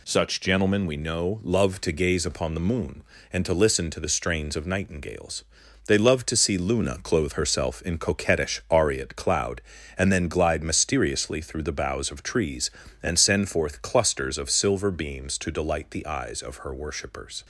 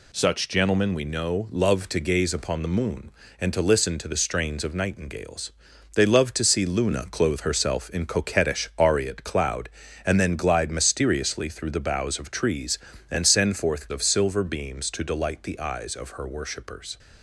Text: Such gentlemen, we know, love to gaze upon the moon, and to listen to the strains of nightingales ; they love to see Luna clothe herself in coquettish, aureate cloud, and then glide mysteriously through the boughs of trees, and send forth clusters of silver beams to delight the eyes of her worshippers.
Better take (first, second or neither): first